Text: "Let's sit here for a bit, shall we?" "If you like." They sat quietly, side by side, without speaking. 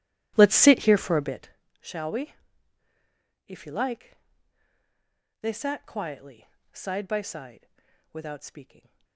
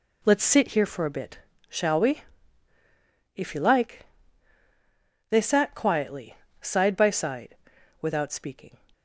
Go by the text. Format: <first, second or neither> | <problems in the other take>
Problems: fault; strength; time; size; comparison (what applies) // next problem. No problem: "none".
second | starts louder than the rest; strong; until 1.6 s; 13.5 dB